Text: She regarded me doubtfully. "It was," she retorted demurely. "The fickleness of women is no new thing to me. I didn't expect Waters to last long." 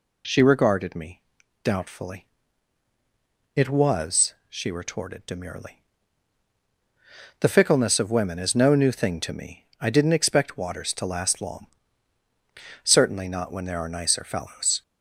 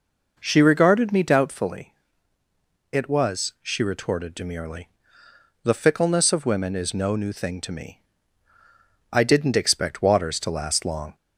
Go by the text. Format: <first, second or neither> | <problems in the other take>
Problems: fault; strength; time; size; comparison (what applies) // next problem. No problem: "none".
second | pauses between "me" and "doubtfully"; at 1.2 s; 0.40 s long // goes on to say "Certainly not when there are nicer fellows"; strong; from 12.8 s on; 2.0 s long